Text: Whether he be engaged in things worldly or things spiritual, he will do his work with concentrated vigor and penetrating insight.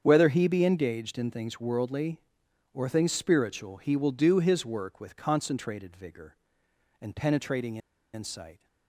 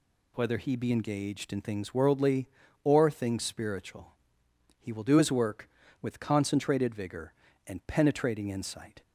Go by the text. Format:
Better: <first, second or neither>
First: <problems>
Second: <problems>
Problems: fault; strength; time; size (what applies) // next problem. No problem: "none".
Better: second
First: starts louder than the rest; strong; until 1.0 s; 7.5 dB // pauses between "penetrating" and "insight"; slight; at 7.7 s; 0.36 s long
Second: none